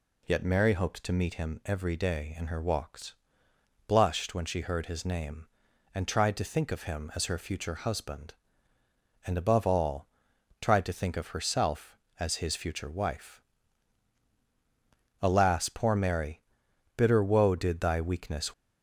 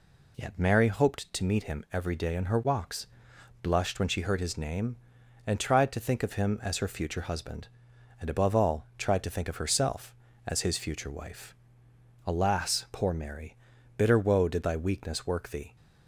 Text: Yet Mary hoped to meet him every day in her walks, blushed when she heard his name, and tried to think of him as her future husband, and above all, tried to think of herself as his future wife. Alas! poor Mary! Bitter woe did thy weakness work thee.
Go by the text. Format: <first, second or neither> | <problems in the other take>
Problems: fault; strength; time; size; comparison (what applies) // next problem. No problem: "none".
second | stops before "work thee"; at 18.5 s